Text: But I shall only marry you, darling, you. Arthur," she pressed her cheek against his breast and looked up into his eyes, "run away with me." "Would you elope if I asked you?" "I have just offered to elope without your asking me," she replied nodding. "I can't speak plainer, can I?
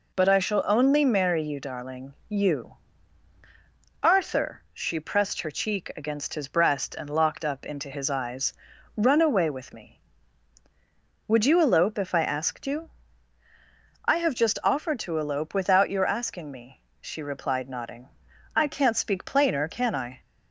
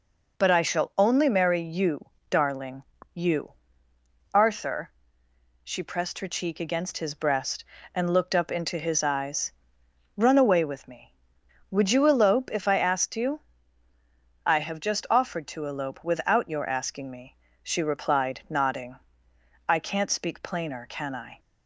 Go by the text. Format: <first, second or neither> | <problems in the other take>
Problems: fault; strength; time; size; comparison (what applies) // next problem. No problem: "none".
second | says "locked" for "looked"; at 7.0 s